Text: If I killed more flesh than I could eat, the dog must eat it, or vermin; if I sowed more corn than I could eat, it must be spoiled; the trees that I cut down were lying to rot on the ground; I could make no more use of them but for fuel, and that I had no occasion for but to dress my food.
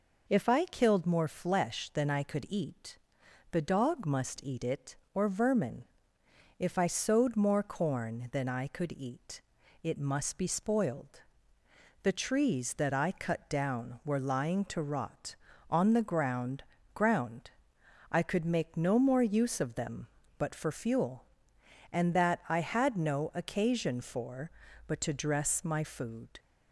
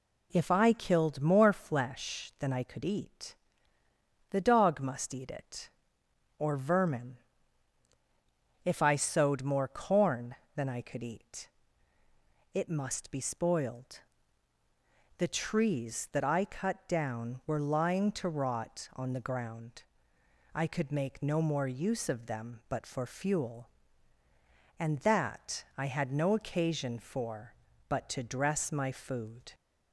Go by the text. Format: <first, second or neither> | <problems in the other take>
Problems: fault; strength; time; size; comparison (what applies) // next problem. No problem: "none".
second | says "ground" twice; at 16.9 s